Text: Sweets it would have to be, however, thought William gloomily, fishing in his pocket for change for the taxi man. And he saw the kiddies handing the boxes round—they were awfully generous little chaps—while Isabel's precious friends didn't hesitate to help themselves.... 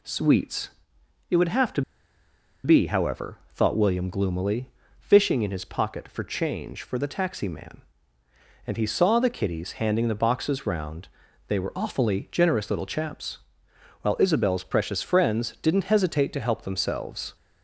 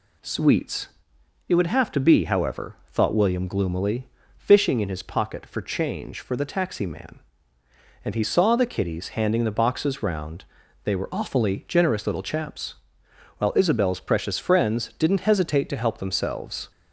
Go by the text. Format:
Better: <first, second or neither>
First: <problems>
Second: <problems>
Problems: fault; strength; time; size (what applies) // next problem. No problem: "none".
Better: second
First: pauses between "Sweets" and "it"; noticeable; at 0.6 s; 0.60 s long // pauses between "to" and "be"; noticeable; at 1.8 s; 0.83 s long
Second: pauses between "Sweets" and "it"; noticeable; at 0.8 s; 0.60 s long